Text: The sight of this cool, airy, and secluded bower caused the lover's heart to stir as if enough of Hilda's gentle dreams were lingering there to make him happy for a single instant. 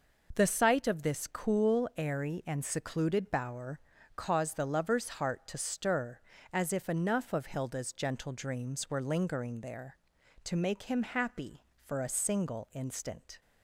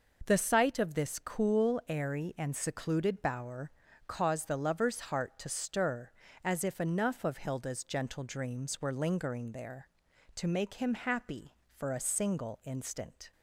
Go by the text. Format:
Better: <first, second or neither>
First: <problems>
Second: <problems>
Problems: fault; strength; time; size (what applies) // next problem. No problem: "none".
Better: neither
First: pauses between "bower" and "caused"; slight; at 3.8 s; 0.34 s long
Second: pauses between "bower" and "caused"; slight; at 3.7 s; 0.34 s long